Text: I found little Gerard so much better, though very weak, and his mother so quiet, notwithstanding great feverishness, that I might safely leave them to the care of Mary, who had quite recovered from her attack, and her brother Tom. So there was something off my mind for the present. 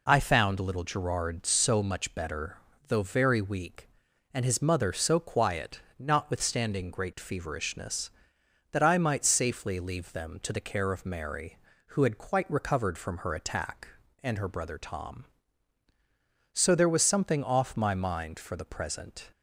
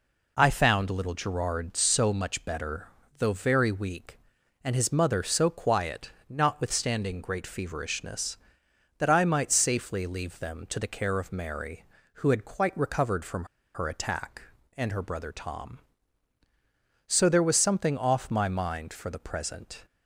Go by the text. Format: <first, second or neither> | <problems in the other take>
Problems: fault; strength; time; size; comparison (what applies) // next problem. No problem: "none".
first | pauses between "from" and "her"; slight; at 13.4 s; 0.29 s long